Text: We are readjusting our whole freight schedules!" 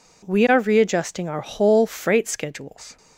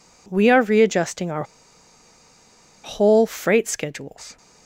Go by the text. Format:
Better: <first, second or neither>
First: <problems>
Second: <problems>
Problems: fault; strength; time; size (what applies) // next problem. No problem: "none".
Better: first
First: none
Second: pauses between "our" and "whole"; strong; at 1.4 s; 1.4 s long